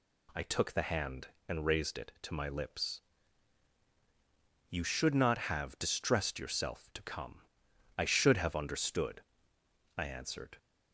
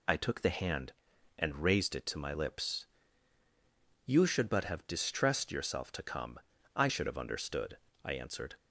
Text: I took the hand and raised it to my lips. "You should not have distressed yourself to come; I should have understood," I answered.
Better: first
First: none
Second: says "but" for "not"; at 4.5 s

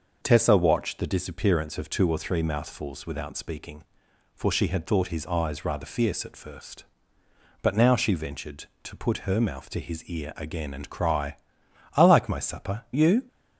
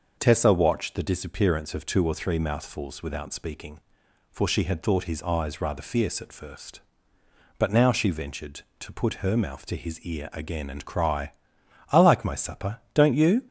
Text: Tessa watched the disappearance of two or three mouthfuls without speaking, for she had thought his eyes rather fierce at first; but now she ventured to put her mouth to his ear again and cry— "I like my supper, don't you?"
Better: second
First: starts louder than the rest; noticeable; until 1.2 s; 6 dB // skips "don't"; at 12.8 s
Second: starts louder than the rest; noticeable; until 1.1 s; 6 dB

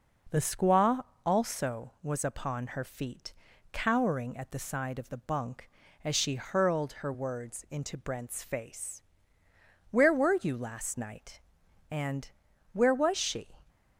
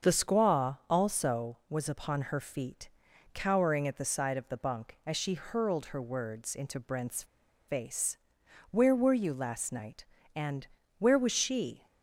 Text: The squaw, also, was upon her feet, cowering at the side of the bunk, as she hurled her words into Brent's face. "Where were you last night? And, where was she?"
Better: first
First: none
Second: starts louder than the rest; until 1.1 s; 6.5 dB // pauses between "Brent's" and "face"; at 7.2 s; 0.44 s long

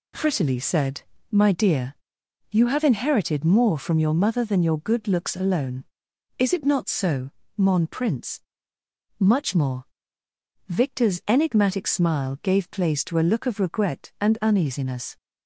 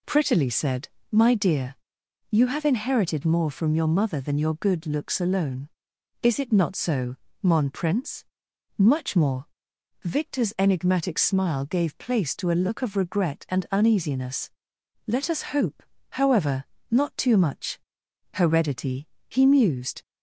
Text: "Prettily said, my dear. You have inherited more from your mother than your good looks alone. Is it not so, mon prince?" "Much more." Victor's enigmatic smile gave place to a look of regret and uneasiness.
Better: first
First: none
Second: goes on to say "Let us hope however not too much Heredity he mused"; strong; from 15.0 s on; 4.9 s long

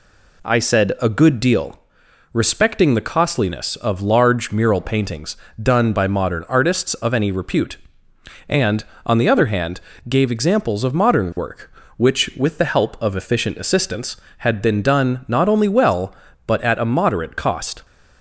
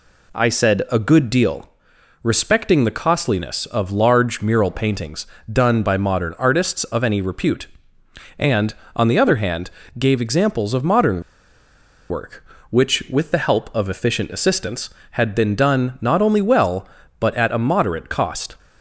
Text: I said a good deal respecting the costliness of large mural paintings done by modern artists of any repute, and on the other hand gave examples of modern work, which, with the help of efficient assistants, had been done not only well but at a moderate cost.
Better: first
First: pauses between "deal" and "respecting"; noticeable; at 1.7 s; 0.56 s long // pauses between "paintings" and "done"; slight; at 5.3 s; 0.24 s long // pauses between "hand" and "gave"; slight; at 9.8 s; 0.28 s long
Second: pauses between "deal" and "respecting"; noticeable; at 1.6 s; 0.56 s long // pauses between "paintings" and "done"; slight; at 5.2 s; 0.24 s long // pauses between "hand" and "gave"; slight; at 9.7 s; 0.28 s long // pauses between "modern" and "work"; noticeable; at 11.2 s; 0.89 s long

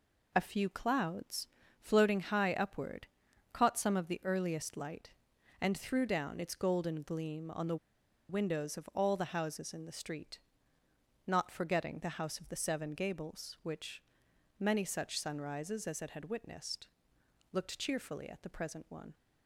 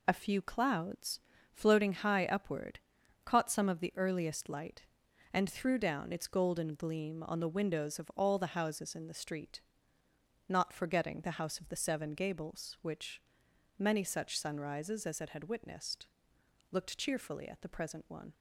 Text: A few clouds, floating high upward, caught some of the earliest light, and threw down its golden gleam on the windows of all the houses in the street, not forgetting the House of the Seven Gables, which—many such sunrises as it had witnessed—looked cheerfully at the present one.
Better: second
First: pauses between "the" and "windows"; noticeable; at 7.7 s; 0.53 s long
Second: none

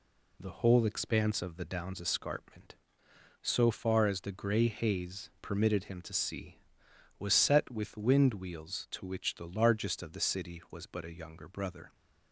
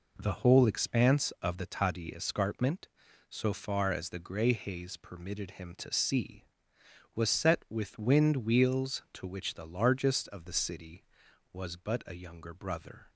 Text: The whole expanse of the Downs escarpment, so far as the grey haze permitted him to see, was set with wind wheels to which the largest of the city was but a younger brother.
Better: first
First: none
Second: says "Tadi" for "Downs"; at 1.6 s

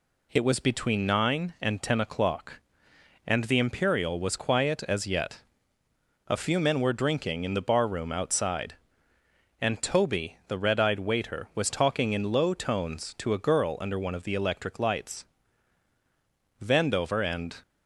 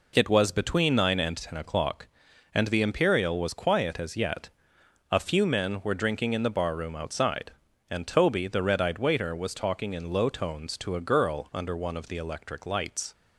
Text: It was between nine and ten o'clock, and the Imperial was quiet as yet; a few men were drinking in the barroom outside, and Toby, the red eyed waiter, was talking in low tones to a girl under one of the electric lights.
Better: second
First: goes on to say "Vandover and"; noticeable; from 16.6 s on; 1.0 s long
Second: none

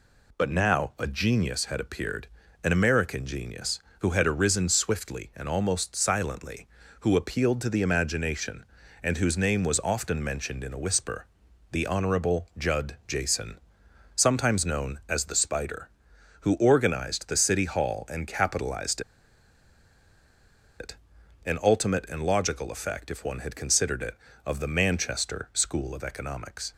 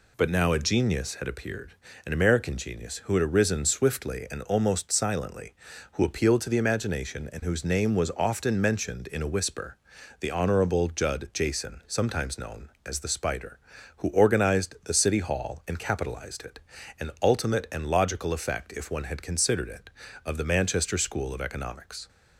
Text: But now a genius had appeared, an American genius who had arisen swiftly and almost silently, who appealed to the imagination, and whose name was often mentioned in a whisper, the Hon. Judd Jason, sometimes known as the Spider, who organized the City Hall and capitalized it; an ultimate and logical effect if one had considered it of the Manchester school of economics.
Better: second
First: pauses between "capitalized" and "it"; strong; at 19.0 s; 1.7 s long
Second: none

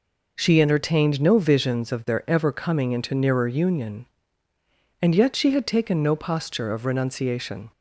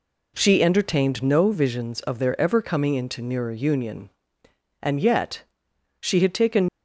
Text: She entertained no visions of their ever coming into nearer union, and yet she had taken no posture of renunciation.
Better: first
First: none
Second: pauses between "yet" and "she"; noticeable; at 5.4 s; 0.58 s long // stops before "no posture of renunciation"; at 6.6 s

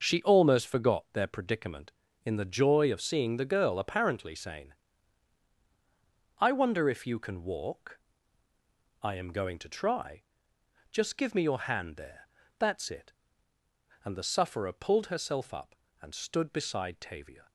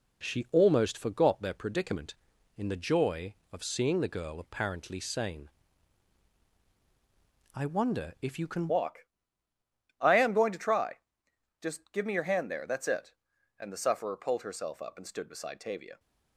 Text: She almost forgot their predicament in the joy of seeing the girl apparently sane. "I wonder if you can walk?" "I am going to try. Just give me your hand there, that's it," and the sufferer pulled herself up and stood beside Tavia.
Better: first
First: none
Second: changes voice at "walk"; from 8.6 s on; 7.3 s long

